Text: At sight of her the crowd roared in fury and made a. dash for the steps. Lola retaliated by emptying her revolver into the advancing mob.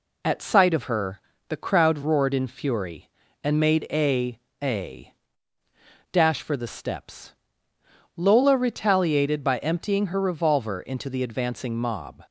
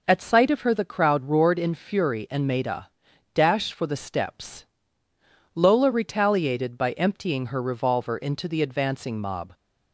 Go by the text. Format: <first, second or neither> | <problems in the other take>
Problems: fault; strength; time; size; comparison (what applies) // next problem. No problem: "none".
second | pauses between "her" and "the"; slight; at 1.2 s; 0.26 s long // says "a" twice; at 4.6 s